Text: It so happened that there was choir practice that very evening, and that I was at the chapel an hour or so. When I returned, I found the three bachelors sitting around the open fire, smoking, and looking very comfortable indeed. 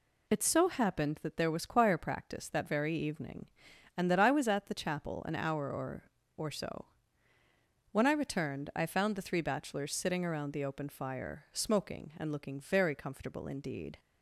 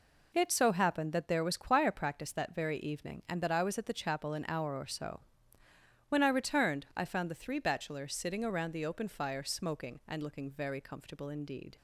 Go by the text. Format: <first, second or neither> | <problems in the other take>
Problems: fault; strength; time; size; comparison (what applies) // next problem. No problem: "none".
second | says "or" twice; at 6.3 s